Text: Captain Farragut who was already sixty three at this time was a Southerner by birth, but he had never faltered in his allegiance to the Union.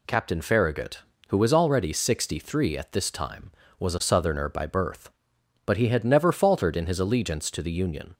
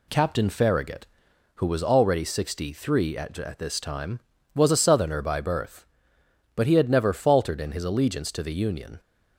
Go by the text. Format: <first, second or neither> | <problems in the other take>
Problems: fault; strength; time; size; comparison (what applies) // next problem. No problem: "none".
first | says "at" twice; at 3.3 s